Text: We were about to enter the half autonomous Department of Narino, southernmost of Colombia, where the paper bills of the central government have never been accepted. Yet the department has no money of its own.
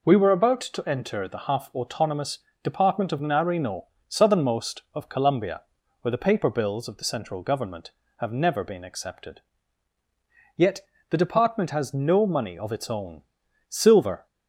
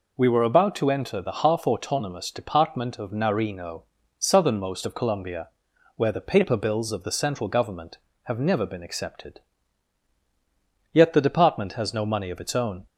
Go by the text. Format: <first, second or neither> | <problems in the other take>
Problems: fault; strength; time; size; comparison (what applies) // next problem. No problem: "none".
second | pauses between "autonomous" and "Department"; slight; at 2.3 s; 0.24 s long // pauses between "Yet" and "the"; slight; at 10.8 s; 0.30 s long // goes on to say "Silver"; from 13.6 s on; 0.58 s long